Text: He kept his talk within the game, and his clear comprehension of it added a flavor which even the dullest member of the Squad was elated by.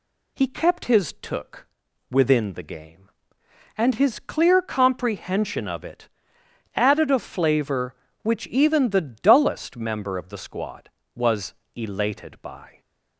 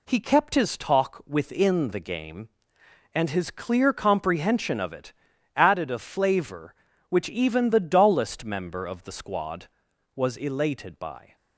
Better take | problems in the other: second | says "took" for "talk"; at 1.2 s // pauses between "it" and "added"; noticeable; at 6.0 s; 0.66 s long; also in the second // pauses between "was" and "elated"; slight; at 11.5 s; 0.22 s long

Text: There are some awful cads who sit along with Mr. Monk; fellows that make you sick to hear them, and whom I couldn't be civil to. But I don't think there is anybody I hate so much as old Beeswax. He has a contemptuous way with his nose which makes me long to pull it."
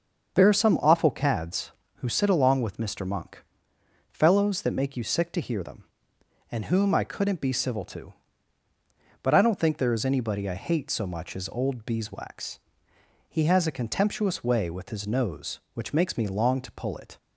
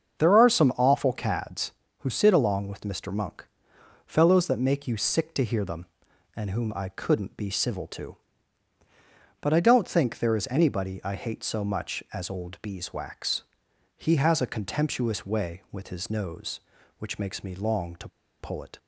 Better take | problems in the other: first | starts louder than the rest; until 1.2 s; 7 dB; also in the first // pauses between "to" and "pull"; slight; at 18.0 s; 0.32 s long

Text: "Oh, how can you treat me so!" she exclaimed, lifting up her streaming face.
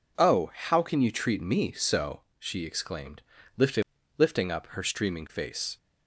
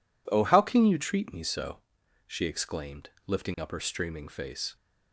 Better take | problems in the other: second | says "lifting" twice; at 4.1 s

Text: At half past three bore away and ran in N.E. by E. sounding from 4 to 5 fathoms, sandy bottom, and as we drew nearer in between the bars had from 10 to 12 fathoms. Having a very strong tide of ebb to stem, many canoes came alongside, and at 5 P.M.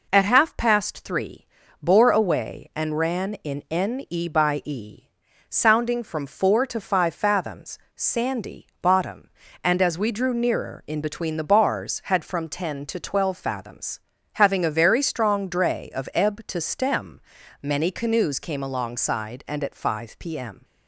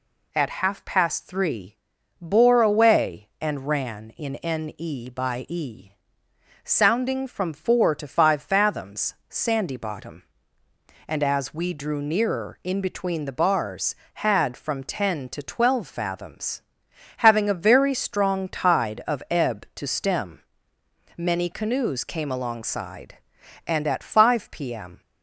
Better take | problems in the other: second | pauses between "three" and "bore"; slight; at 1.4 s; 0.36 s long; also in the second // says "dray" for "tide"; at 15.4 s

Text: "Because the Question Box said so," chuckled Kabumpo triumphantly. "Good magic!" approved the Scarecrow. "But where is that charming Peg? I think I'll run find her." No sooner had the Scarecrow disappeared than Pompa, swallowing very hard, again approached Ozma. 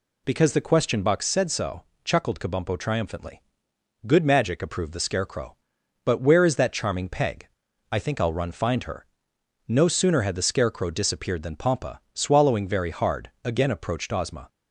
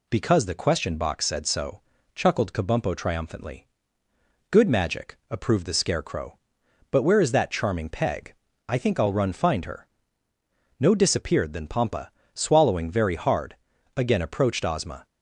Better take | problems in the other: first | skips "sooner had the Scarecrow"; at 10.9 s

